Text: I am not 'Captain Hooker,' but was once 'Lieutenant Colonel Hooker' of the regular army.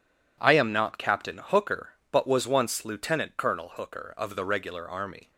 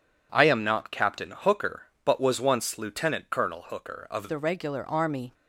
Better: first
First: none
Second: changes voice at "the"; from 4.2 s on; 1.1 s long

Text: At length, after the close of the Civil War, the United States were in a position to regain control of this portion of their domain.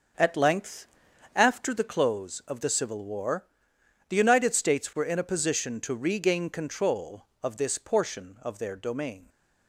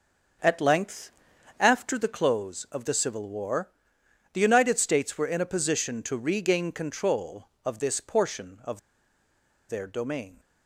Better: first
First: starts louder than the rest; until 1.6 s; 6.5 dB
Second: starts louder than the rest; until 1.8 s; 6.5 dB // pauses between "of" and "their"; noticeable; at 8.7 s; 0.89 s long

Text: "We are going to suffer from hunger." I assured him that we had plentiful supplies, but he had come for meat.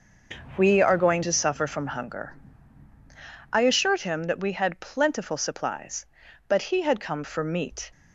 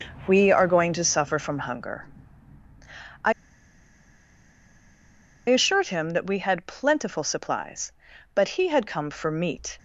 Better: first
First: starts louder than the rest; until 1.5 s; 6.5 dB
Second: starts louder than the rest; until 1.2 s; 6.5 dB // pauses between "I" and "assured"; strong; at 3.3 s; 2.1 s long

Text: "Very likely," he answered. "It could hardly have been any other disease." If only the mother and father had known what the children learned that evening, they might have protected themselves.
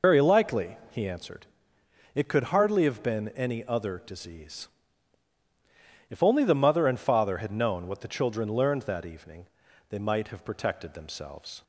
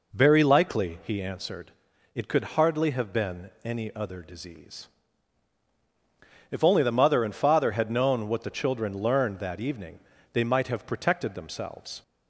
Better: second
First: loses the start of "Very"; at 0.0 s; 50 ms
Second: none

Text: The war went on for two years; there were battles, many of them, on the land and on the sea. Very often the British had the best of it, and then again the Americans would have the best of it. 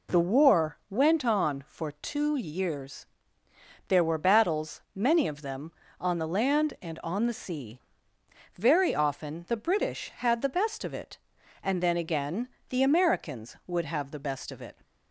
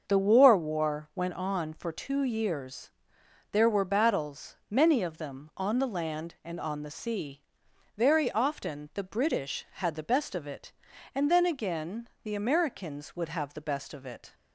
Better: first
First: pauses between "again" and "the"; slight; at 12.4 s; 0.22 s long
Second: starts louder than the rest; until 1.0 s; 6.5 dB // says "war" twice; at 0.5 s // pauses between "again" and "the"; slight; at 12.0 s; 0.16 s long

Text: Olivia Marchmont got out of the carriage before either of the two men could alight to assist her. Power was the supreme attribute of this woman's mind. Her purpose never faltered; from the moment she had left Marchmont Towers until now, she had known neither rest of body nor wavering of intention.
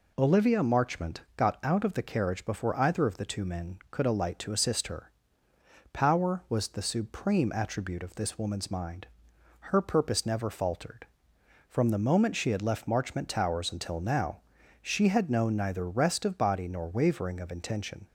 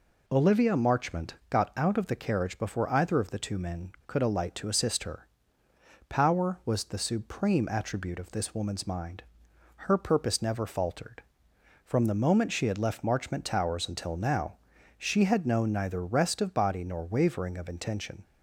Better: neither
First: pauses between "Marchmont" and "got"; slight; at 1.2 s; 0.16 s long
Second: pauses between "Marchmont" and "got"; slight; at 1.3 s; 0.16 s long

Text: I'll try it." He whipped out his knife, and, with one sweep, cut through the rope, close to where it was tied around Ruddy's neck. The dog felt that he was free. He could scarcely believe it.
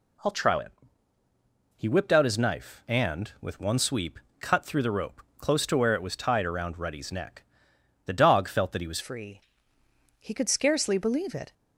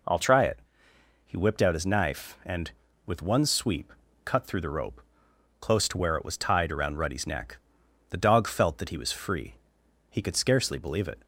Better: second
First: changes voice at "free"; from 8.9 s on; 2.6 s long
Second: none

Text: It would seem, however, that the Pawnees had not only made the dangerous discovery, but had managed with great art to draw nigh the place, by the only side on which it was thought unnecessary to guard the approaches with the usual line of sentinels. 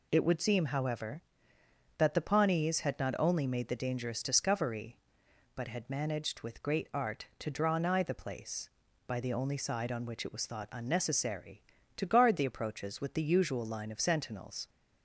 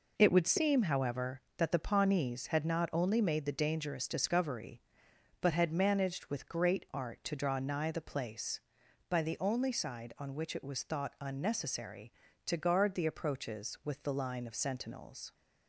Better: first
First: none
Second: skips "usual"; at 14.1 s

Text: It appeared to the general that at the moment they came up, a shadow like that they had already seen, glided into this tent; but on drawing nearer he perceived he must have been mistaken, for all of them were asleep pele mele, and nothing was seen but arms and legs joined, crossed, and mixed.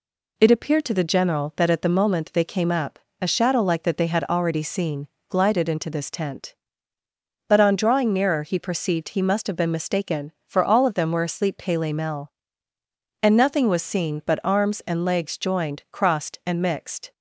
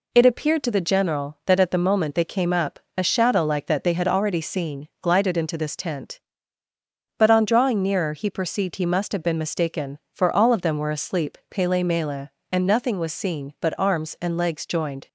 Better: first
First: none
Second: stops before "crossed and mixed"; at 15.0 s

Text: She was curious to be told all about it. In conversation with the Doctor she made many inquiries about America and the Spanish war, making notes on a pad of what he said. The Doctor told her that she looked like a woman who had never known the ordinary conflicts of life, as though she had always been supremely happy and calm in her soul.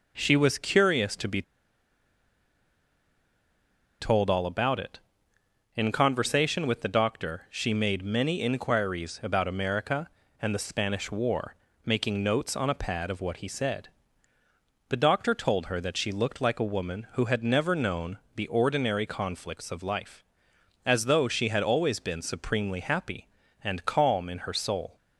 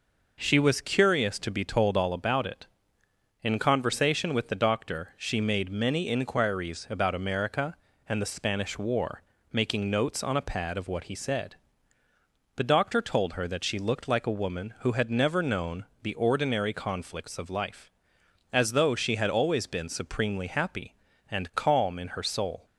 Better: second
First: pauses between "be" and "told"; strong; at 1.4 s; 2.5 s long // pauses between "known" and "the"; slight; at 18.1 s; 0.20 s long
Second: pauses between "known" and "the"; slight; at 15.8 s; 0.20 s long

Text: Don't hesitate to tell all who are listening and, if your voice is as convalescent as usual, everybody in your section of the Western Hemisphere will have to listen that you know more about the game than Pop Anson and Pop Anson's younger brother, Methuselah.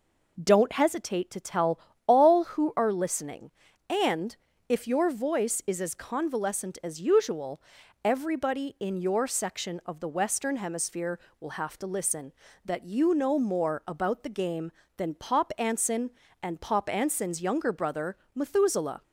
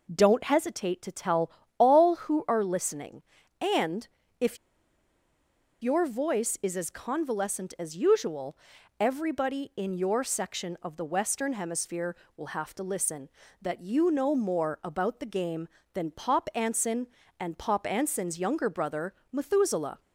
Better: first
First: pauses between "tell" and "all"; slight; at 1.8 s; 0.26 s long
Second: pauses between "tell" and "all"; slight; at 1.5 s; 0.26 s long // pauses between "if" and "your"; strong; at 4.5 s; 1.2 s long

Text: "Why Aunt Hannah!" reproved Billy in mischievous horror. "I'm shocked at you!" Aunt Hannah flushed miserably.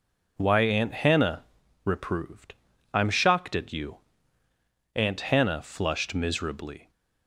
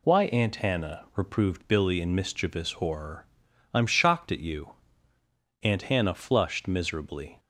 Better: second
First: skips "Billy in mischievous horror"; at 2.7 s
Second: none

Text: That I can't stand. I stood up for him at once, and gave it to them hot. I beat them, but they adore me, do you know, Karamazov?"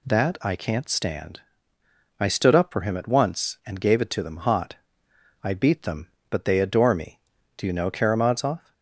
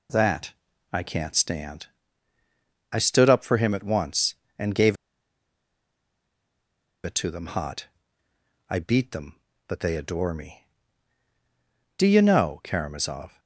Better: first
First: none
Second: pauses between "That" and "I"; at 0.5 s; 0.38 s long // pauses between "gave" and "it"; strong; at 4.9 s; 2.0 s long

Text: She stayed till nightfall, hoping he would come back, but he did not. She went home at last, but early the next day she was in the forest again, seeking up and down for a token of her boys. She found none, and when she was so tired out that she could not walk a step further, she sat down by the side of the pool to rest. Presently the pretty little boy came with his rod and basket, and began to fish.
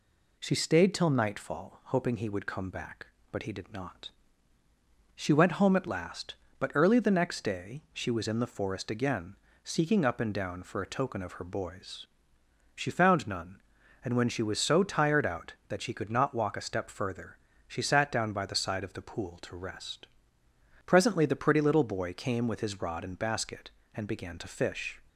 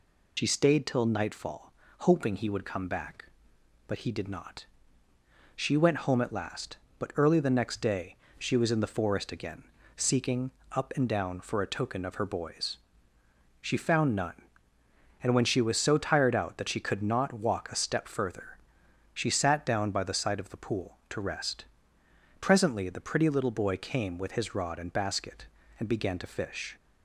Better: first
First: none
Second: loses the start of "She"; at 0.3 s; 45 ms // pauses between "day" and "she"; slight; at 8.1 s; 0.24 s long // pauses between "seeking" and "up"; slight; at 10.4 s; 0.22 s long

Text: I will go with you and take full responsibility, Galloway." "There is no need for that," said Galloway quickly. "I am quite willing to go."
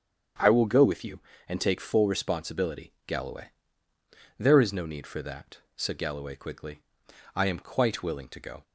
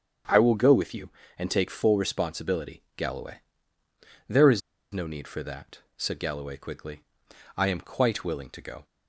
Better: first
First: starts louder than the rest; strong; until 1.6 s; 7.5 dB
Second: starts louder than the rest; strong; until 1.5 s; 8 dB // pauses between "is" and "no"; slight; at 4.6 s; 0.32 s long

